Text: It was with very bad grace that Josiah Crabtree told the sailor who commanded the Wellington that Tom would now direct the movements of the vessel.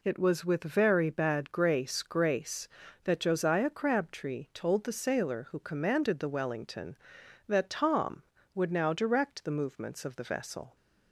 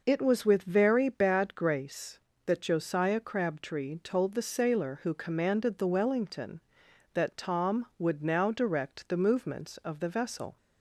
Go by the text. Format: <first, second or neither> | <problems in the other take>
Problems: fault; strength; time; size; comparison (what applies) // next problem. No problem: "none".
second | says "grace" twice; at 2.0 s